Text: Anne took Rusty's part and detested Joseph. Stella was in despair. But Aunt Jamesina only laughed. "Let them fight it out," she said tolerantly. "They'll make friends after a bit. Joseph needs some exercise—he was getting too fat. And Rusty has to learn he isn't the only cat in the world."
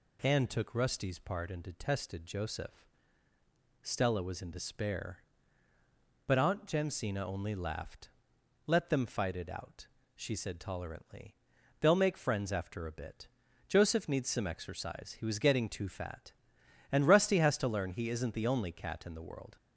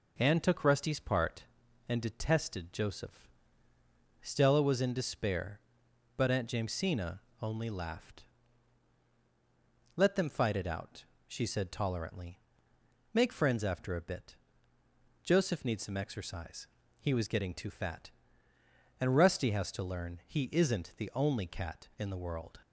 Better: first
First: none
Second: pauses between "Jamesina" and "only"; slight; at 7.1 s; 0.24 s long // skips "They'll"; at 12.7 s

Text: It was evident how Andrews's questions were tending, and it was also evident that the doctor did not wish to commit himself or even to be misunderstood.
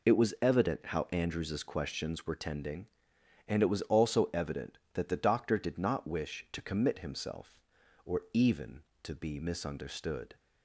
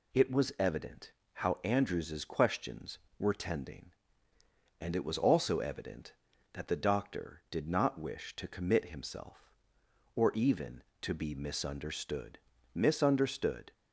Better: first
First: none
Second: pauses between "evident" and "how"; slight; at 1.1 s; 0.22 s long // says "misunderstood" twice; at 12.7 s

